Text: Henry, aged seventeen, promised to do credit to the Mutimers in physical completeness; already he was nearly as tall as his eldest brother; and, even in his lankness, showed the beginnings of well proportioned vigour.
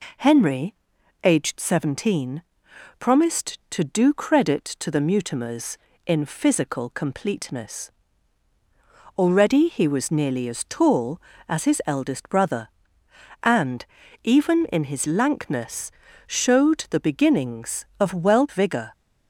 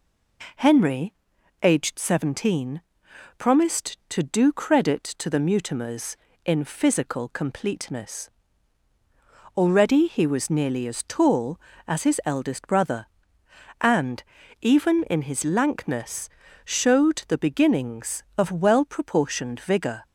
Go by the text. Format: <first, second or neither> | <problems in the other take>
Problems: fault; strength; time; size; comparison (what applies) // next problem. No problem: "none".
second | skips "proportioned"; at 18.4 s